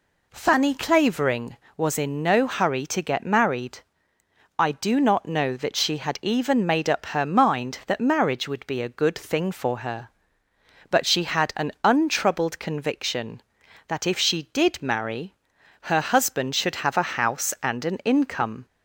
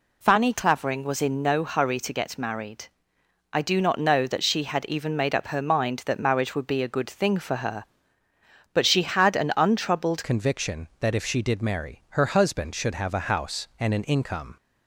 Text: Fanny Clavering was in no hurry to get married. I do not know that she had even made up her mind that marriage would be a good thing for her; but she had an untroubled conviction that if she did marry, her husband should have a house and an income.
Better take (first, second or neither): first